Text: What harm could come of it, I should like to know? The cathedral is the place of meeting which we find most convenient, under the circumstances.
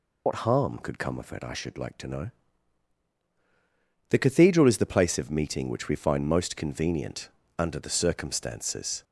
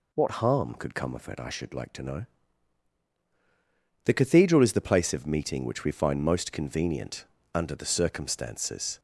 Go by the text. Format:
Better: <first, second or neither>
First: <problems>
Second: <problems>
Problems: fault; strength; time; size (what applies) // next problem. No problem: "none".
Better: second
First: loses the start of "What"; at 0.2 s; 80 ms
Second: none